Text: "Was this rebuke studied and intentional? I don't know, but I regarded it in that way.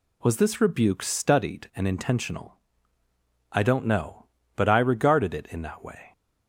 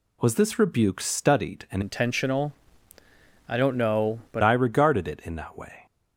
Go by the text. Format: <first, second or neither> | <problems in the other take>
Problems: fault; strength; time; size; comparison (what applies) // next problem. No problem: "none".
first | changes voice from "intentional" to "but"; from 1.8 to 4.4 s; 2.6 s long